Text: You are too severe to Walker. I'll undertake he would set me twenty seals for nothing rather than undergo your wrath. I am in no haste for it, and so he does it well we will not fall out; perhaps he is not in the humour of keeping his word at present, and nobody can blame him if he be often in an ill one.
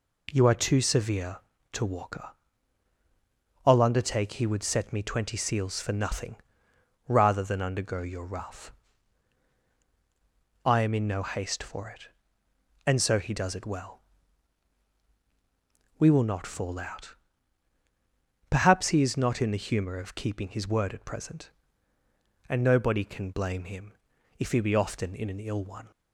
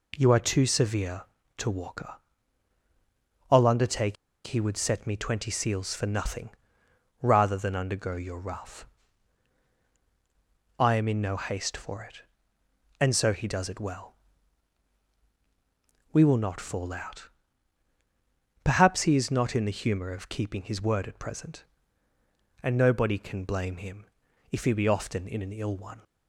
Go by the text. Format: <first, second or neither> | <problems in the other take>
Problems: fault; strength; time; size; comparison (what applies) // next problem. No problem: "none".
first | pauses between "undertake" and "he"; slight; at 4.1 s; 0.31 s long // pauses between "nothing" and "rather"; noticeable; at 6.4 s; 0.72 s long; noticeable in the first // pauses between "well" and "we"; strong; at 14.1 s; 2.0 s long; strong in the first // pauses between "him" and "if"; noticeable; at 24.0 s; 0.46 s long; noticeable in the first